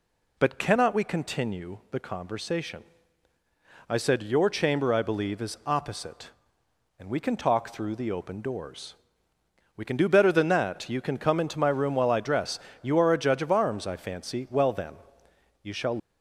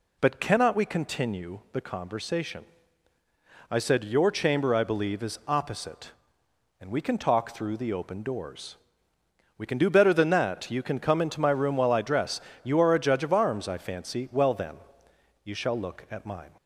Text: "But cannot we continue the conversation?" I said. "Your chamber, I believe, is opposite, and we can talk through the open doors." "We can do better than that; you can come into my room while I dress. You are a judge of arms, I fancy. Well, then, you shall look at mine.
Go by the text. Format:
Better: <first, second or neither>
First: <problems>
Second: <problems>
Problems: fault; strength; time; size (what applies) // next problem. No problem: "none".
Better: second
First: stops before "look at mine"; at 15.9 s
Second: none